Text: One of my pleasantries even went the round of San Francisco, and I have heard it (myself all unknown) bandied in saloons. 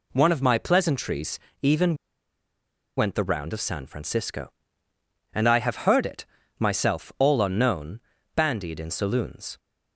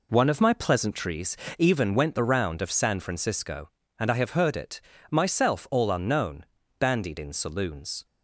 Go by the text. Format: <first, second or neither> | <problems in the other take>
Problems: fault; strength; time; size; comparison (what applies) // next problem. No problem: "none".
second | pauses between "pleasantries" and "even"; slight; at 1.3 s; 0.22 s long; slight in the second // pauses between "even" and "went"; at 1.9 s; 1.0 s long